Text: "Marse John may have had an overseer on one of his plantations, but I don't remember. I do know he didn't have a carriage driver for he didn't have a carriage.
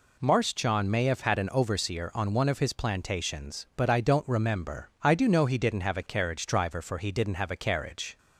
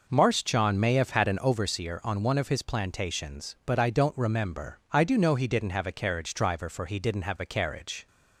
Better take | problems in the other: first | starts louder than the rest; noticeable; until 1.6 s; 5.5 dB

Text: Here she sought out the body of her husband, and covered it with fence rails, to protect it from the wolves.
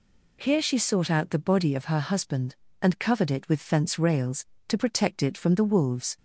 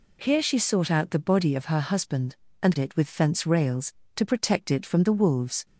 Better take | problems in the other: first | skips "covered"; at 2.7 s

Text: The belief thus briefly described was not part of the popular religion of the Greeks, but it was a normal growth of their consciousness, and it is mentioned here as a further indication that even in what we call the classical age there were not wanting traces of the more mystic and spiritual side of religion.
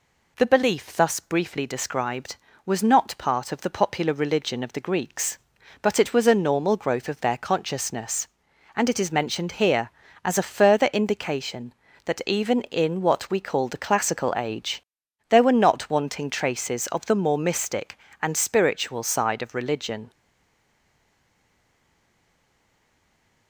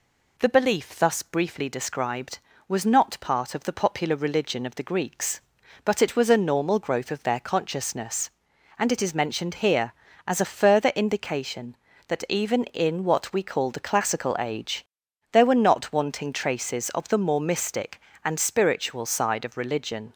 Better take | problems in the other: second | pauses between "age" and "there"; noticeable; at 14.8 s; 0.46 s long; noticeable in the second // stays silent after the last word; strong; from 20.1 s on; 3.3 s long

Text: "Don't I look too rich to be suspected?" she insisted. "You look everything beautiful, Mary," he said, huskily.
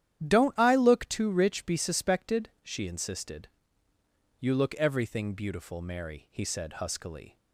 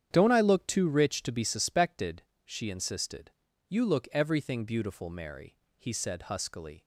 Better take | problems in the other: second | starts louder than the rest; strong; until 1.3 s; 10.5 dB; strong in the second // skips "to"; at 1.6 s

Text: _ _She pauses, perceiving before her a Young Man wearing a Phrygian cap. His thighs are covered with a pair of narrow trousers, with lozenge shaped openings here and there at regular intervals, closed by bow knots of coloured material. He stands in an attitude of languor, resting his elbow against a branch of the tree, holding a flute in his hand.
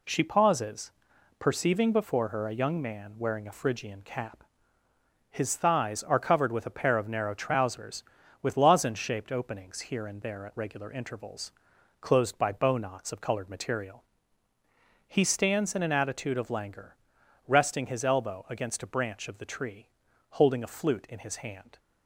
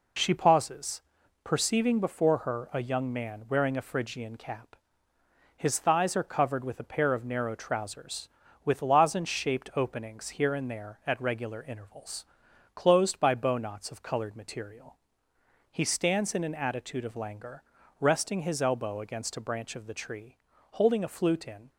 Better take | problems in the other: first | stops before "his hand"; at 21.6 s

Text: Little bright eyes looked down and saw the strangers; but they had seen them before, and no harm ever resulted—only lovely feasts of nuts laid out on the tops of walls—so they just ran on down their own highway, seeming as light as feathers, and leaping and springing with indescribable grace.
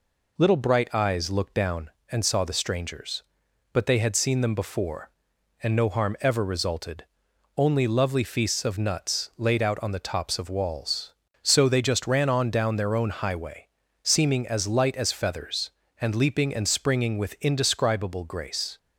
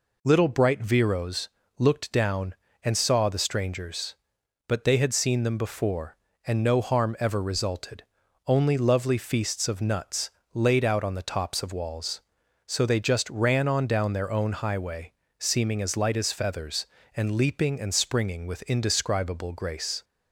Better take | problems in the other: first | says "viros" for "eyes"; at 0.8 s // pauses between "nuts" and "laid"; slight; at 10.2 s; 0.22 s long

